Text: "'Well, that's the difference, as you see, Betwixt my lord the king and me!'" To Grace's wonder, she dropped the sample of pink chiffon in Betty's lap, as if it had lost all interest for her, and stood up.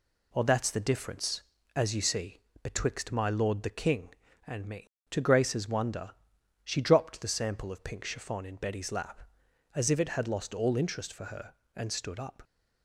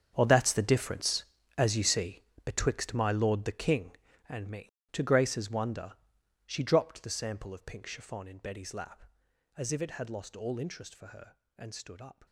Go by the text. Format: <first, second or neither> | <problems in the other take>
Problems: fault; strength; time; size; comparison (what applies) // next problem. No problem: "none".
first | gets quieter; strong; throughout; 15 dB